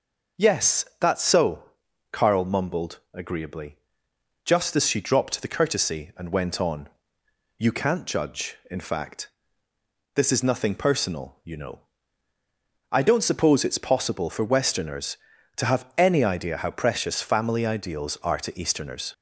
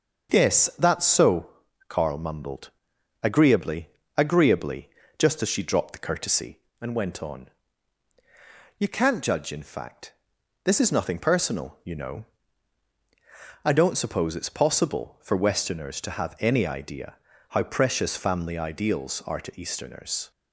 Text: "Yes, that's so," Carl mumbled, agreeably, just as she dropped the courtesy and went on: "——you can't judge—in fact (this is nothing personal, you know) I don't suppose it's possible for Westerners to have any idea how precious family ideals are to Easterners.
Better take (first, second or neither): first